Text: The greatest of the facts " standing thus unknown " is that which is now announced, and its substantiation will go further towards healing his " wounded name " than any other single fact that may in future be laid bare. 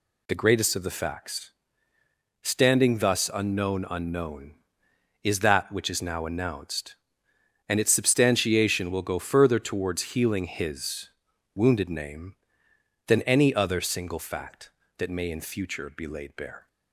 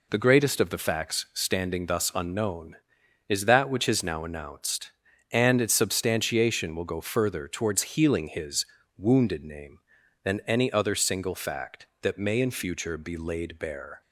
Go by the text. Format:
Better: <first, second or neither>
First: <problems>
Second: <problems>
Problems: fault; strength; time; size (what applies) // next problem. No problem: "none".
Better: second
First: says "unknown" twice; at 3.8 s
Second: none